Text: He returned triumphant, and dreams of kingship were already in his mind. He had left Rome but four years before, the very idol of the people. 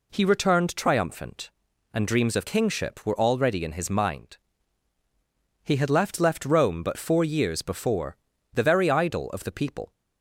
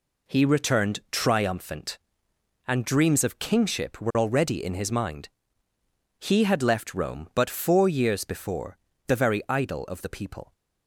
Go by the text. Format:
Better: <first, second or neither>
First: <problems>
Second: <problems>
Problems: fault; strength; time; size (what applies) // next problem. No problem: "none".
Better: second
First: says "left" twice; at 6.1 s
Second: none